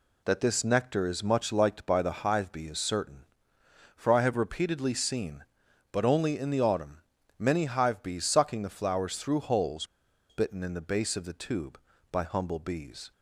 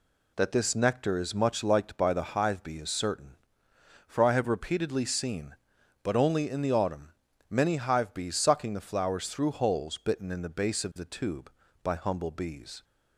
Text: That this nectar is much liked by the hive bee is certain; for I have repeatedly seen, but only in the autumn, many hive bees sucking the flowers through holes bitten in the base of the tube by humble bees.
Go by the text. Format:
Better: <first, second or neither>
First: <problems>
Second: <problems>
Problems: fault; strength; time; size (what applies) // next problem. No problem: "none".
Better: second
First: pauses between "holes" and "bitten"; at 9.8 s; 0.44 s long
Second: none